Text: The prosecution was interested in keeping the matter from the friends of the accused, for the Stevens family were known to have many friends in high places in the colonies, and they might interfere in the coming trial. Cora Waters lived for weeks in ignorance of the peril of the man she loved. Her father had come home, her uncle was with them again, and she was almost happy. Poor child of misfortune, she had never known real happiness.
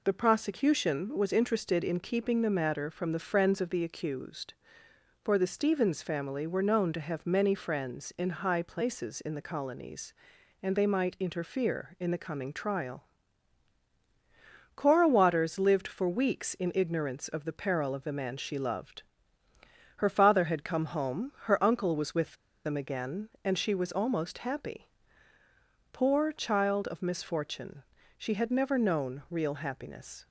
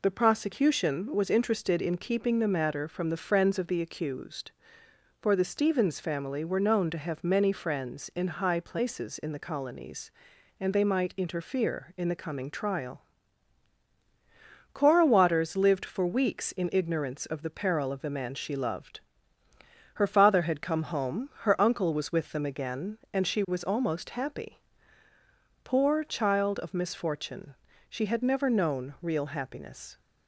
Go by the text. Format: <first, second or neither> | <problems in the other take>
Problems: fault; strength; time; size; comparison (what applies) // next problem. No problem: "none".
second | pauses between "with" and "them"; slight; at 22.3 s; 0.30 s long